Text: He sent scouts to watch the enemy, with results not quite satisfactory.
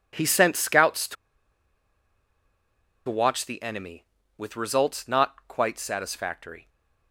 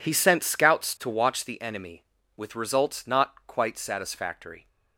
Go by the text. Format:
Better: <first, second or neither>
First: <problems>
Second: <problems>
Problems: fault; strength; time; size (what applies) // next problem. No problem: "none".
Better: second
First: pauses between "to" and "watch"; strong; at 1.1 s; 1.9 s long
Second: none